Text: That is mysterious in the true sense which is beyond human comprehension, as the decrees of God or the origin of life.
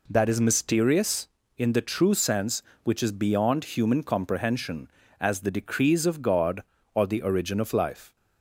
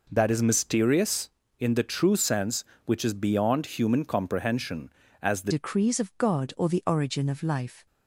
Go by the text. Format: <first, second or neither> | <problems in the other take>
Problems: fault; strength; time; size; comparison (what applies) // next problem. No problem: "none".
first | changes voice at "decrees"; from 5.4 s on; 2.4 s long